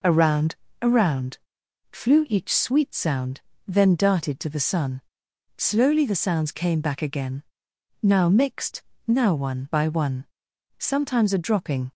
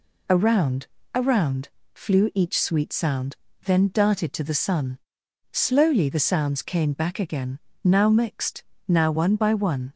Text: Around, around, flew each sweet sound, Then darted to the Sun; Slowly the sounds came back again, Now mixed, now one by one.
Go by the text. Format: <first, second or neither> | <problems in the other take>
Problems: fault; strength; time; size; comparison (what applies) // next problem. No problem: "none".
second | goes on to say "Sometimes a dropping"; noticeable; from 10.7 s on; 1.1 s long